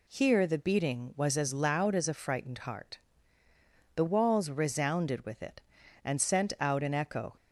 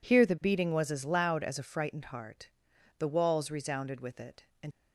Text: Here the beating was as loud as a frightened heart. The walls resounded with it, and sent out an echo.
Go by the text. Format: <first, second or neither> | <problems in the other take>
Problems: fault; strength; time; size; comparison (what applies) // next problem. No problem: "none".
first | stops before "sent out an echo"; at 4.7 s